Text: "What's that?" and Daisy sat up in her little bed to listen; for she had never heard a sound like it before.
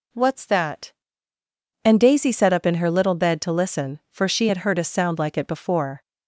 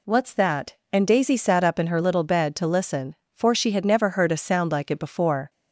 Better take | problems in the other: second | skips "never"; at 4.6 s

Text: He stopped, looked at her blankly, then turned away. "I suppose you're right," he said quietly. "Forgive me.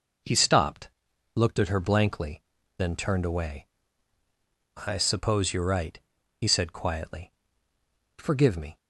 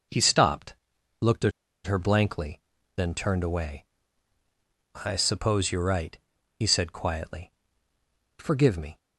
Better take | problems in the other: first | pauses between "at" and "her"; slight; at 1.5 s; 0.33 s long

